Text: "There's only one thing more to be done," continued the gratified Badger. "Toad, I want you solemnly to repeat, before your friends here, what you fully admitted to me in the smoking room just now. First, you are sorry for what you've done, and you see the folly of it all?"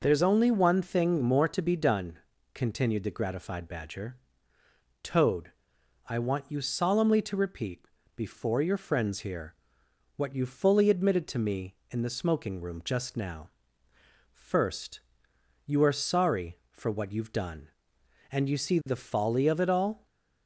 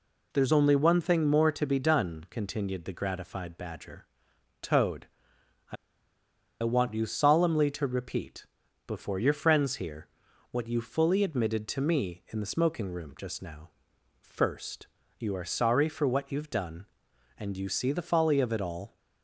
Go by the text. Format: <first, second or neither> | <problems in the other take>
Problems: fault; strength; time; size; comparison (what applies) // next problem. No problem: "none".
first | pauses between "I" and "want"; noticeable; at 5.7 s; 0.87 s long